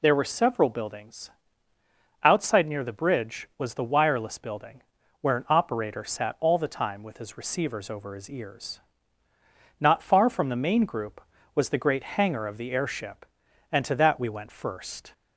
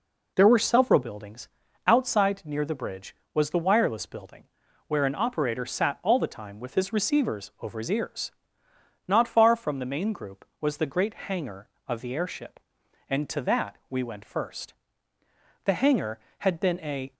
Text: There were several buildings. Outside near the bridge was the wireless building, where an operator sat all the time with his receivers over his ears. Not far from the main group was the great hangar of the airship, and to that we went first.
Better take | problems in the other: first | goes on to say "The hangar had been a"; from 15.6 s on; 1.4 s long

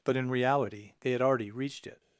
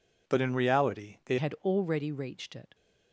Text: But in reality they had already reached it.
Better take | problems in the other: first | changes voice at "had"; from 1.3 s on; 1.4 s long

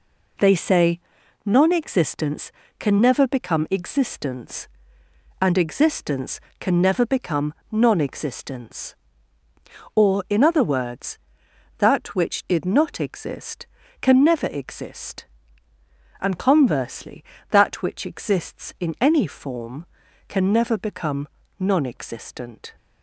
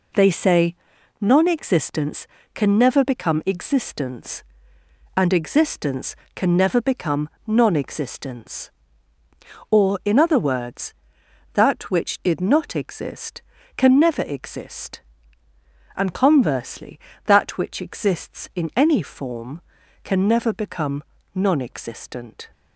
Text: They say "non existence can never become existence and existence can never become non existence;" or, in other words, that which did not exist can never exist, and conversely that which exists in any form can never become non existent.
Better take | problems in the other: neither | pauses between "say" and "non"; the same in both // pauses between "become" and "non"; slight; the same in both // pauses between "become" and "non"; slight; the same in both

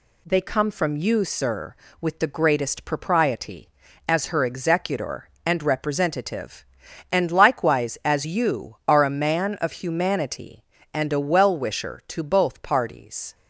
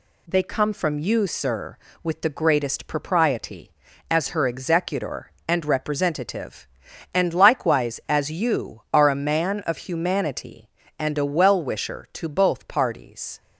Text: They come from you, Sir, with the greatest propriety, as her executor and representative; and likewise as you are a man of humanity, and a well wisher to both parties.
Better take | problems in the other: neither | none

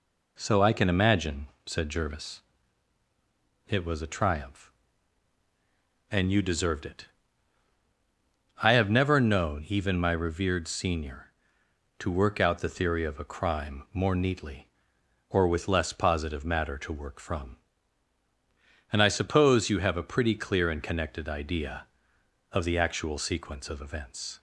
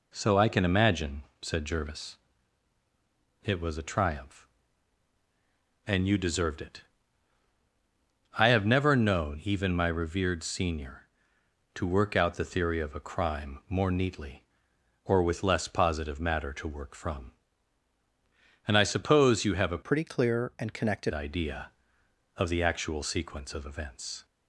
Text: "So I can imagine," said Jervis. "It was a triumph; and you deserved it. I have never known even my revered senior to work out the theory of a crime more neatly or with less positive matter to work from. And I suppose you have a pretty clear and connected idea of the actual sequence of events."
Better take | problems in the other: first | changes voice from "pretty" to "connected"; from 19.8 to 21.1 s; 1.3 s long

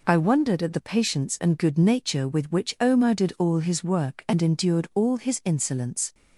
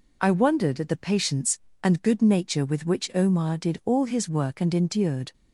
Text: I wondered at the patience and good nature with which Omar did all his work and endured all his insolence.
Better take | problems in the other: first | stops before "all his insolence"; at 5.3 s

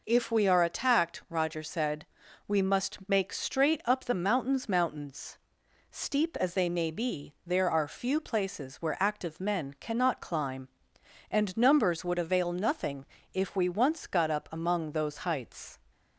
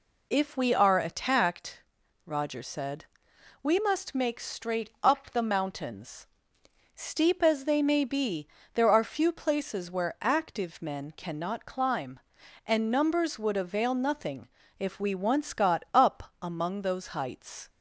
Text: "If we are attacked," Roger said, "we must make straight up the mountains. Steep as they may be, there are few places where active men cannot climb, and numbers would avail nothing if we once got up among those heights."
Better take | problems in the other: second | says "mountains" twice; at 4.6 s // pauses between "nothing" and "if"; slight; at 13.0 s; 0.26 s long; slight in the second

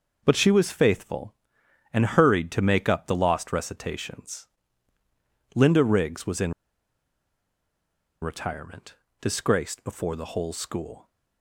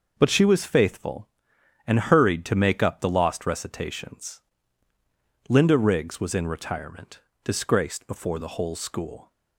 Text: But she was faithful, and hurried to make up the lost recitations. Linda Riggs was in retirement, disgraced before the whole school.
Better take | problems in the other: second | pauses between "in" and "retirement"; strong; at 6.5 s; 1.6 s long

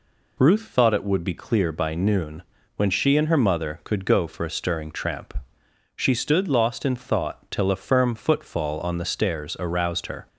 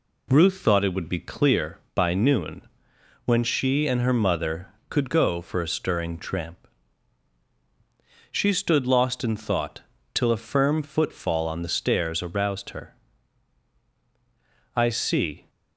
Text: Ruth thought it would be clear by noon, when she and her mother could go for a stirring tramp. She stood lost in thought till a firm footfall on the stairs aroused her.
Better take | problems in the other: first | pauses between "thought" and "till"; slight; at 9.8 s; 0.32 s long // goes on to say "I see"; noticeable; from 14.7 s on; 0.74 s long

